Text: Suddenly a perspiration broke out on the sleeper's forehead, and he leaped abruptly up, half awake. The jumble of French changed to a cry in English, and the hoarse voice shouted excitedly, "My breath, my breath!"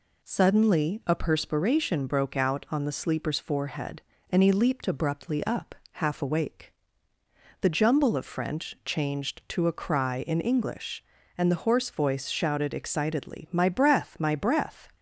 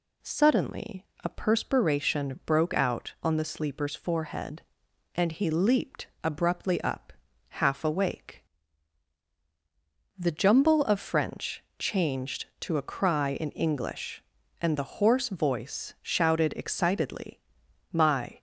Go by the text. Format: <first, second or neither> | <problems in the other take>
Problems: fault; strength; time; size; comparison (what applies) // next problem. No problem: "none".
first | pauses between "Suddenly" and "a"; slight; at 1.0 s; 0.18 s long // pauses between "leaped" and "abruptly"; slight; at 6.0 s; 0.16 s long // pauses between "French" and "changed"; slight; at 11.6 s; 0.16 s long // stops before "breath my breath"; at 18.3 s